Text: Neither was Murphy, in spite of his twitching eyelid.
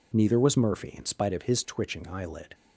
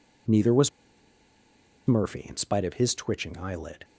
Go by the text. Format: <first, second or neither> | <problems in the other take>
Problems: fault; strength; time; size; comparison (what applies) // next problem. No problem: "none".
first | pauses between "was" and "Murphy"; at 0.6 s; 1.1 s long